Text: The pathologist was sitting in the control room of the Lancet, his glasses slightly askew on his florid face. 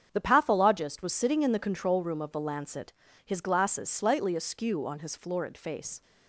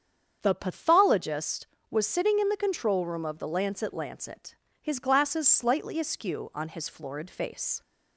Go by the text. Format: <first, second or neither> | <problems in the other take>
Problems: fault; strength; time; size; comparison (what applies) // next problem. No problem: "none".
first | starts louder than the rest; strong; until 1.4 s; 7.5 dB; strong in the first // says "Lancet" twice; at 3.9 s